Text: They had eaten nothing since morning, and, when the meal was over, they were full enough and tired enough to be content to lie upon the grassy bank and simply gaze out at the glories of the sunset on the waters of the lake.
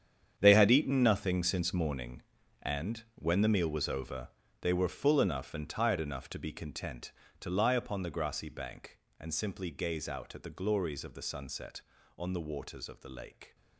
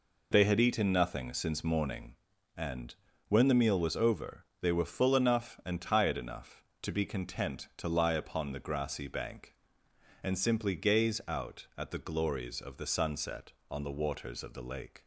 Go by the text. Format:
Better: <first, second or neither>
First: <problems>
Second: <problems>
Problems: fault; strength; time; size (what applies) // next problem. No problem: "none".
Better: second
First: gets quieter; strong; throughout; 13 dB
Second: none